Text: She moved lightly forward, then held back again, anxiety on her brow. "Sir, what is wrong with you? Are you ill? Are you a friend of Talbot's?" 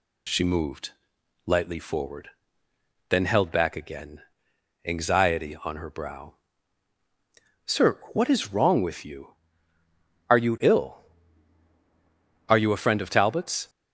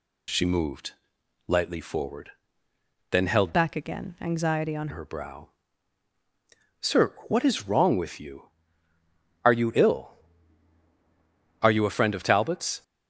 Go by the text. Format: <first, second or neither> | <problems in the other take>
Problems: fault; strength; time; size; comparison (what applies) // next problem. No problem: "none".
first | pauses between "moved" and "lightly"; noticeable; at 0.9 s; 0.56 s long; noticeable in the first // changes voice from "back" to "on"; from 3.5 to 4.8 s; 1.3 s long